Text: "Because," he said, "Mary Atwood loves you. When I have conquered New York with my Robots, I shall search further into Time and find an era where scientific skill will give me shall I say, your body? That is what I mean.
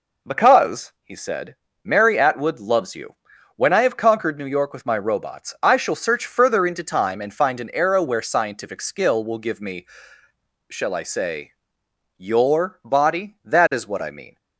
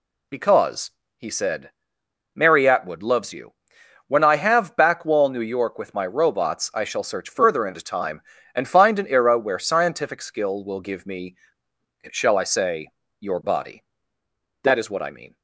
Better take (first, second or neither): first